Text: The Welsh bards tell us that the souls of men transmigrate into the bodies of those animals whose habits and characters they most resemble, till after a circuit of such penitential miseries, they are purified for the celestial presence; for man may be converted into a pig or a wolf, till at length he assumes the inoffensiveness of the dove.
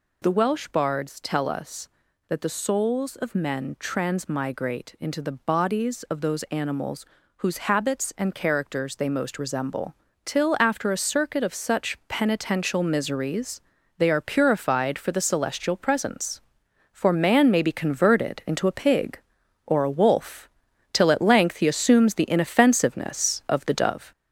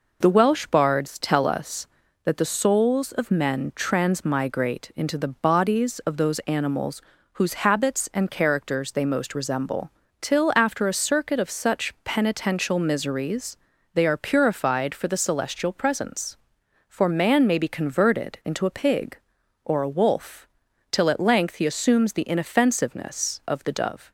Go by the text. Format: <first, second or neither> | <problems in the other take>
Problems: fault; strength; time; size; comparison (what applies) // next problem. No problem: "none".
second | gets louder; noticeable; throughout; 4.5 dB // pauses between "animals" and "whose"; slight; at 7.0 s; 0.32 s long; slight in the second